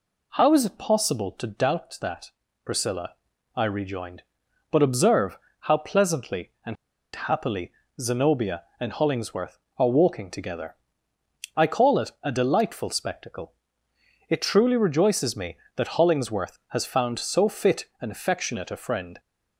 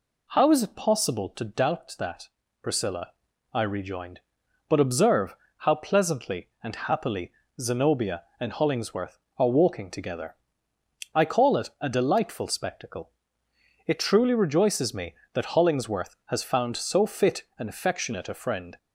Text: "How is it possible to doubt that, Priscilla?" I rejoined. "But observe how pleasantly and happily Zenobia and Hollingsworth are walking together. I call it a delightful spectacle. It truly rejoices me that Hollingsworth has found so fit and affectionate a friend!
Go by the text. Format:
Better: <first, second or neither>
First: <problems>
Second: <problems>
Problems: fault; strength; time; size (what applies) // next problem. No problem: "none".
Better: second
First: pauses between "observe" and "how"; slight; at 5.4 s; 0.22 s long // pauses between "and" and "happily"; at 6.7 s; 0.40 s long // pauses between "happily" and "Zenobia"; slight; at 7.7 s; 0.26 s long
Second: pauses between "observe" and "how"; slight; at 5.3 s; 0.22 s long // pauses between "happily" and "Zenobia"; slight; at 7.3 s; 0.26 s long